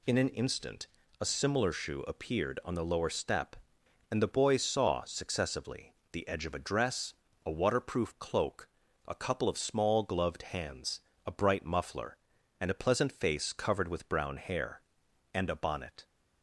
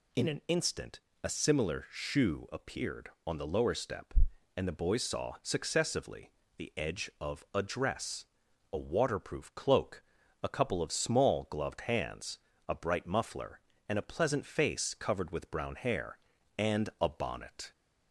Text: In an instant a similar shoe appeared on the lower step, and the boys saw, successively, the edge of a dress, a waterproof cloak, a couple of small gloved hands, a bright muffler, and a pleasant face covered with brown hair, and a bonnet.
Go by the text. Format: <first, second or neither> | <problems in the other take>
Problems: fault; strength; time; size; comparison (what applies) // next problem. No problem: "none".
neither | pauses between "instant" and "a"; slight; the same in both